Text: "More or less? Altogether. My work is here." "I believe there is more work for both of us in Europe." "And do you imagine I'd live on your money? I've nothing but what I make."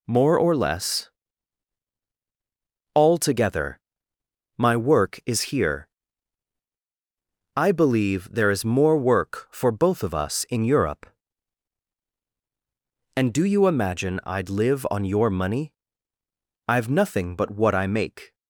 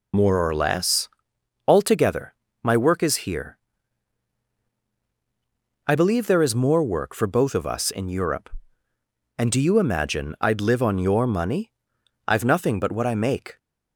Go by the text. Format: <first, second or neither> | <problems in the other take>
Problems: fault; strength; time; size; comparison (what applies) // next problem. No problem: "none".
first | loses the start of "More"; at 0.1 s; 65 ms